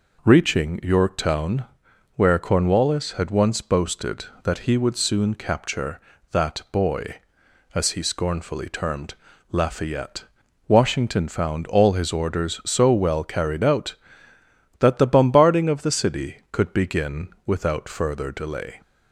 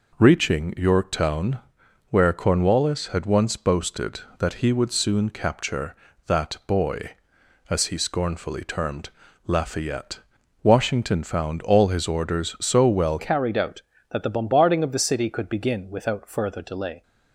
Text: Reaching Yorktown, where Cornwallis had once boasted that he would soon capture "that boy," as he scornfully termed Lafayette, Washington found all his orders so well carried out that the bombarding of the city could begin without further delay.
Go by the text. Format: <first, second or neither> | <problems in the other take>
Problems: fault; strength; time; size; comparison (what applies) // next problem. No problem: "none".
first | pauses between "termed" and "Lafayette"; at 9.0 s; 0.38 s long; also in the first // changes voice at "carried"; from 13.1 s on; 3.9 s long